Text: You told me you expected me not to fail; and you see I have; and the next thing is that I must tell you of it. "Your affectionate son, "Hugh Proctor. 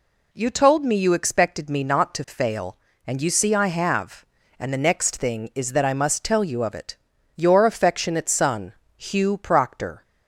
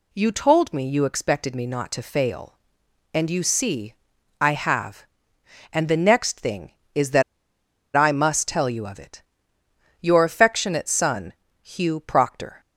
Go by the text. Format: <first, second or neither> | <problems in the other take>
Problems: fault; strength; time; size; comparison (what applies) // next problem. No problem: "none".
first | pauses between "see" and "I"; noticeable; at 3.9 s; 0.48 s long // pauses between "that" and "I"; noticeable; at 7.2 s; 0.73 s long